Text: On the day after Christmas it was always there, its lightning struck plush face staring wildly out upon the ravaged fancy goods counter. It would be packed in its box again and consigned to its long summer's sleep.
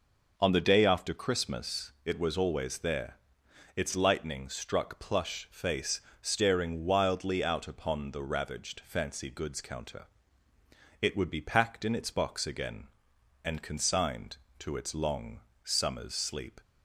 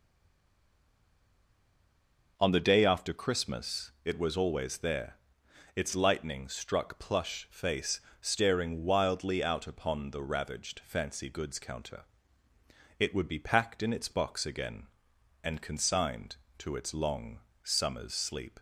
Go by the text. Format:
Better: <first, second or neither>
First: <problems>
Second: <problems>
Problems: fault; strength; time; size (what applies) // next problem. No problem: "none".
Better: first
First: pauses between "face" and "staring"; slight; at 6.0 s; 0.18 s long // pauses between "long" and "summer's"; slight; at 15.3 s; 0.24 s long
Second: stays silent before the first word; until 2.3 s; 2.3 s long // pauses between "face" and "staring"; slight; at 8.0 s; 0.18 s long // pauses between "long" and "summer's"; slight; at 17.3 s; 0.24 s long